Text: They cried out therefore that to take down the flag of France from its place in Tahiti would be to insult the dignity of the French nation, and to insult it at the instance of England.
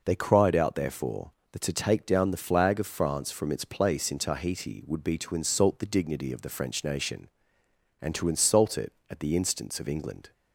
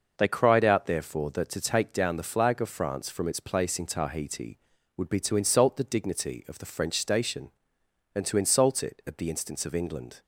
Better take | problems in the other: first | says "station" for "nation"; at 6.9 s

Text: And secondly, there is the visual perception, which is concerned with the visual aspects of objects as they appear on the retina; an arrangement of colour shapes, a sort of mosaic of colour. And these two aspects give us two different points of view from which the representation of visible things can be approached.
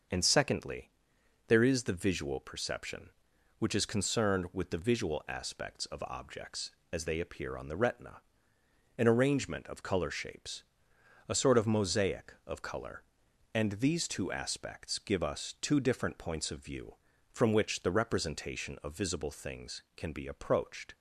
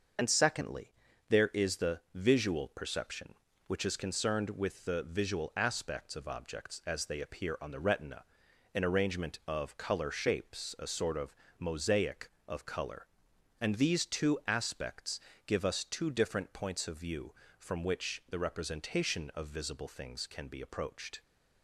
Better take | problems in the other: first | loses the start of "And"; at 0.1 s; 45 ms // starts louder than the rest; until 1.6 s; 6.5 dB; noticeable in the first // pauses between "of" and "mosaic"; slight; at 11.3 s; 0.24 s long // pauses between "aspects" and "give"; slight; at 15.1 s; 0.28 s long

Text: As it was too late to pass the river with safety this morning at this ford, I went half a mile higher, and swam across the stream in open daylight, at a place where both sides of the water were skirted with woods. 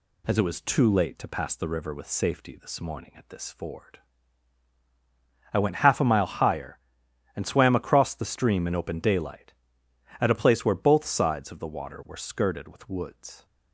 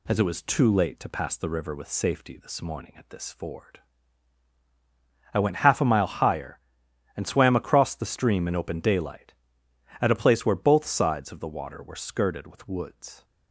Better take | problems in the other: neither | none

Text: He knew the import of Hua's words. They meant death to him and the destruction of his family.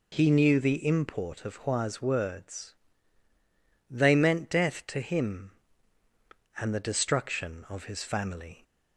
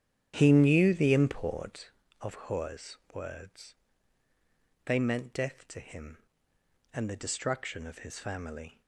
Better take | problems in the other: first | starts louder than the rest; strong; until 1.9 s; 9.5 dB // pauses between "Hua's" and "words"; slight; at 2.9 s; 0.16 s long

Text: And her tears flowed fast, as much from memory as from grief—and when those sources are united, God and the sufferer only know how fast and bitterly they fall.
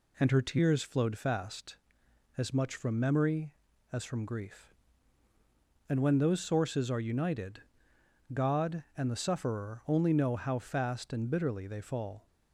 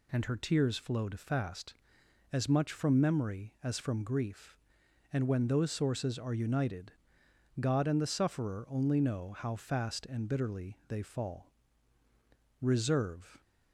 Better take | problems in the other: first | goes on to say "Reserve"; noticeable; from 12.6 s on; 0.80 s long

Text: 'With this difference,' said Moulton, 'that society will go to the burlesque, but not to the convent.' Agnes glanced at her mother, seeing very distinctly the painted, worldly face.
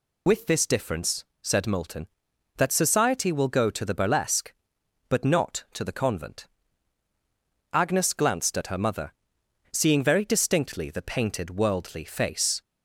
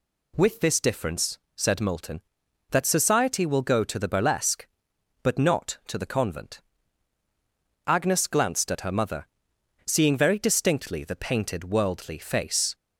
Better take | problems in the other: second | loses the start of "With"; at 0.2 s; 65 ms

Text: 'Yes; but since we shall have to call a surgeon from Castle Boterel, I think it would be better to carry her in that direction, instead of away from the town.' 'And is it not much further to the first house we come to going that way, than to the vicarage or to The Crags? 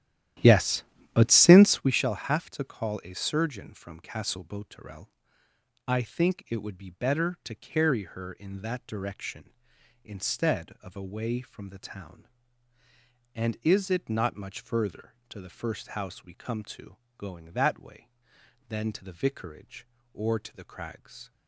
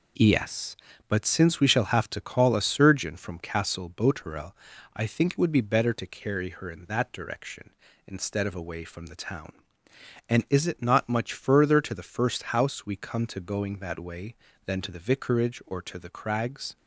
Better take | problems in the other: second | starts louder than the rest; strong; until 1.9 s; 12.5 dB // pauses between "to" and "going"; slight; at 16.9 s; 0.20 s long

